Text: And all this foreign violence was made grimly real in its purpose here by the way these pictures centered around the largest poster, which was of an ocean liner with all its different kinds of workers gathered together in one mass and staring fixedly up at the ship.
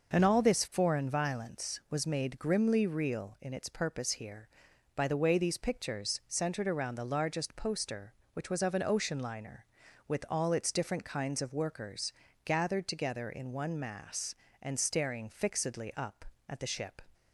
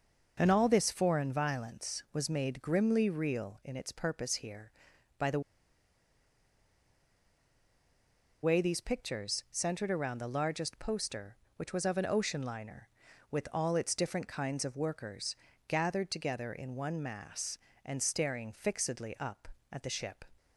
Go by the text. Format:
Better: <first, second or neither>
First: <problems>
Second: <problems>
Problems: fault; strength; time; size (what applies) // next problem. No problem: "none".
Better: first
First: pauses between "workers" and "gathered"; slight; at 12.1 s; 0.32 s long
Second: pauses between "the" and "way"; strong; at 5.4 s; 3.0 s long // pauses between "workers" and "gathered"; slight; at 15.3 s; 0.32 s long